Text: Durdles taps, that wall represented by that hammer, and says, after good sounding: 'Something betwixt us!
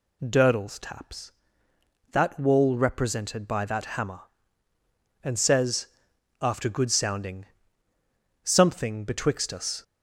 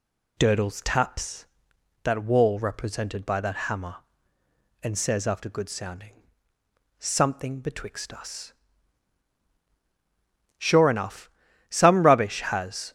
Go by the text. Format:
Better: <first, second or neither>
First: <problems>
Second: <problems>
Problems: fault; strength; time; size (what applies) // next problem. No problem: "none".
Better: first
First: none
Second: goes on to say "Sure enough some rubbish has"; strong; from 10.5 s on; 2.3 s long